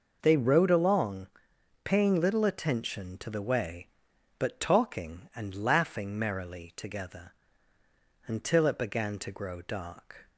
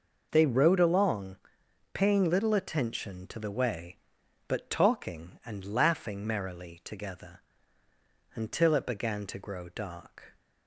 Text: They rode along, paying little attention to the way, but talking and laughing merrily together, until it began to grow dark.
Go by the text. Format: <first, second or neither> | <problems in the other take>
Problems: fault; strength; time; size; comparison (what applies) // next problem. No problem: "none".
neither | none